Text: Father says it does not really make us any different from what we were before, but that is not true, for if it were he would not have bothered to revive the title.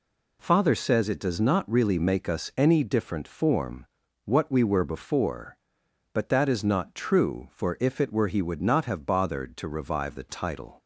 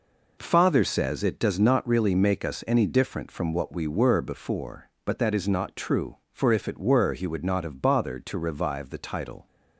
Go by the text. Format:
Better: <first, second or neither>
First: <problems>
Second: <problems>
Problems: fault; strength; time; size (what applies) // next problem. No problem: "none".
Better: second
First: says "form" for "from"; at 3.2 s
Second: none